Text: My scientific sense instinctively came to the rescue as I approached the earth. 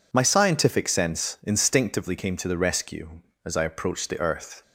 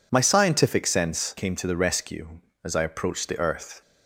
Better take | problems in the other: first | skips "instinctively"; at 1.3 s

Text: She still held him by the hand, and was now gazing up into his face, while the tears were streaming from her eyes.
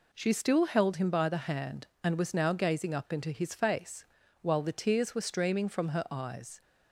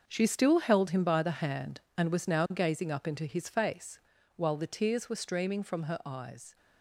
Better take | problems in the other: first | gets quieter; strong; throughout; 11 dB

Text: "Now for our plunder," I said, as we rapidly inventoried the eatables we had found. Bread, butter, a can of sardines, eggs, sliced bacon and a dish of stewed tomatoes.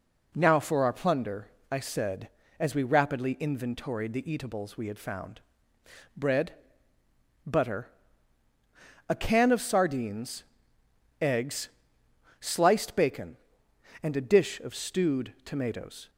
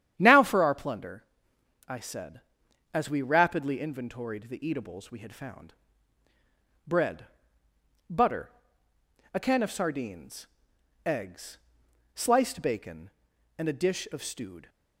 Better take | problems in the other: first | starts louder than the rest; strong; until 1.1 s; 10 dB // stops before "tomatoes"; at 14.6 s

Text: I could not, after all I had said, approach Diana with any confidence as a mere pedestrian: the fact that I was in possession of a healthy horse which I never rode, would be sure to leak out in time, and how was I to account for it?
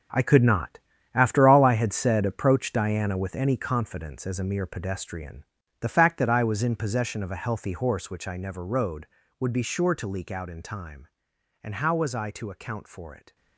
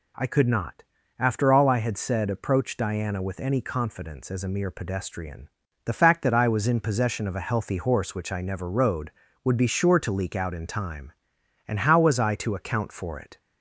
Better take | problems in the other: second | gets quieter; strong; throughout; 11 dB

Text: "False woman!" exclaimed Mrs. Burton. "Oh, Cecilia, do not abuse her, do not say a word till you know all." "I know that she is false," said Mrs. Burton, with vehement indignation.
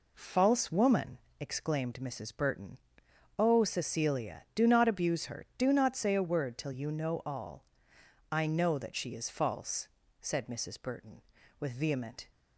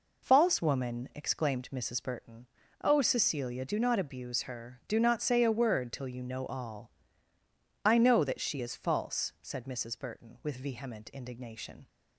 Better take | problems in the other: second | stops before "indignation"; at 12.3 s

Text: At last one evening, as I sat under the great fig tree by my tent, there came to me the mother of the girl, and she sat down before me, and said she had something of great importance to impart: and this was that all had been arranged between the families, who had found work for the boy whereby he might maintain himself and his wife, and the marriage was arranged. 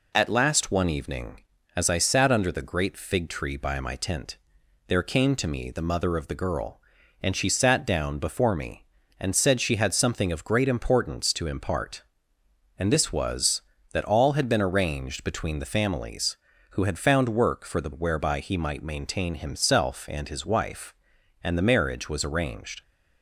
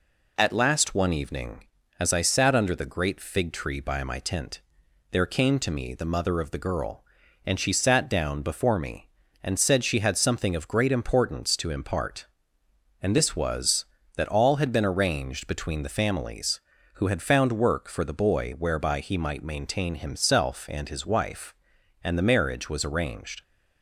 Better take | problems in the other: second | skips "boy"; at 17.9 s

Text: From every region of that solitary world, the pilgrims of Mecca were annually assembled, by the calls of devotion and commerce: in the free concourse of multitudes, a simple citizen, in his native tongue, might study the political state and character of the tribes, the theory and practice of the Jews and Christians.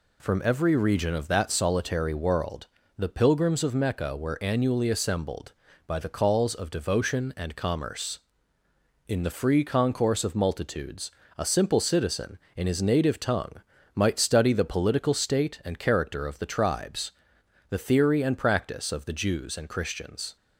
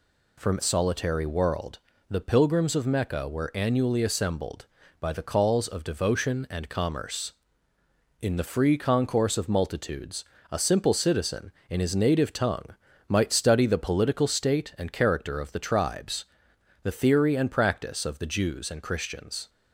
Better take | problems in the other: first | skips "every region of that"; at 0.6 s

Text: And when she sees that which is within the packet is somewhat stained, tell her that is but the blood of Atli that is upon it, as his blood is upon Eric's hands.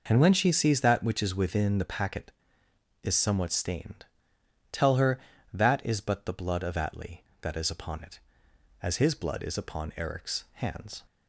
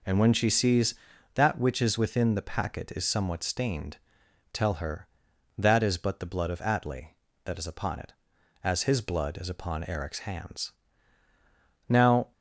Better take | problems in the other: first | goes on to say "Now"; slight; from 11.8 s on; 0.44 s long

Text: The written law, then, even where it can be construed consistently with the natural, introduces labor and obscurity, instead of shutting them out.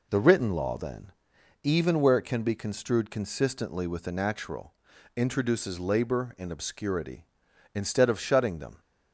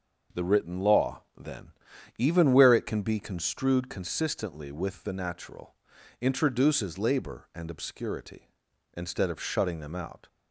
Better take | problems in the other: second | stops before "out"; at 8.7 s

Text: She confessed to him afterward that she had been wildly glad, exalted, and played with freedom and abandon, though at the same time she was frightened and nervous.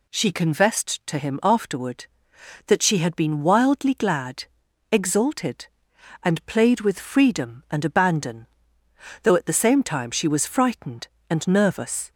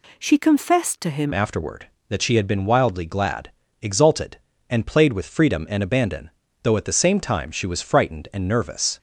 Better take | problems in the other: first | changes voice at "afterward"; from 1.3 s on; 7.6 s long

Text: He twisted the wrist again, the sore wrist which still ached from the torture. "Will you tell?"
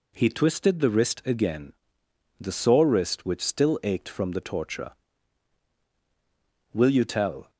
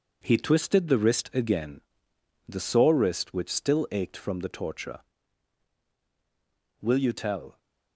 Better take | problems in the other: first | gets quieter; throughout; 6.5 dB

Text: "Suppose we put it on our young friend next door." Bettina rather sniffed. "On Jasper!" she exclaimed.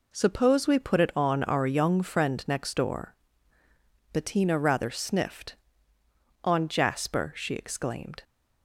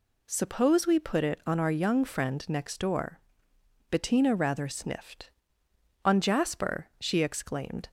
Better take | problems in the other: neither | none

